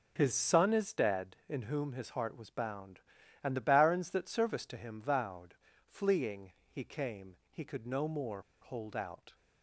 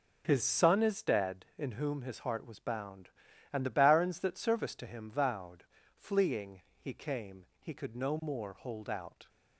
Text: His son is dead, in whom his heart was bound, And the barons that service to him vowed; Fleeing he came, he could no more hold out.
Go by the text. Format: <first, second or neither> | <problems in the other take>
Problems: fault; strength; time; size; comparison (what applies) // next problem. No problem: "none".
second | pauses between "Fleeing" and "he"; slight; at 6.5 s; 0.18 s long; slight in the second // pauses between "more" and "hold"; slight; at 8.4 s; 0.20 s long